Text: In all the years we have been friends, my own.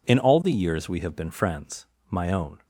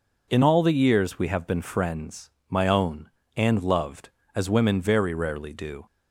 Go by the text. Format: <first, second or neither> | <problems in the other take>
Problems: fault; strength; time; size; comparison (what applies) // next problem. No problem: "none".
first | goes on to say "And loved as women very rarely do"; strong; from 3.3 s on; 2.4 s long